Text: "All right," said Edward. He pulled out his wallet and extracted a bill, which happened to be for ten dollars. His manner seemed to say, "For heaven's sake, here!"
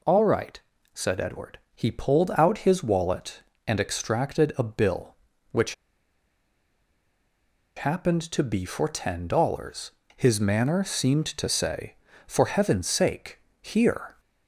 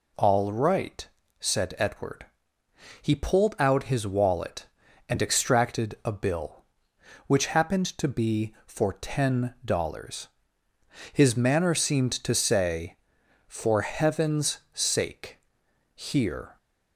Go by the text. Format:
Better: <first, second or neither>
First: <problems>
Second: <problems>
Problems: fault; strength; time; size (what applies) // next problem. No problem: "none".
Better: second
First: pauses between "which" and "happened"; strong; at 5.7 s; 2.0 s long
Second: none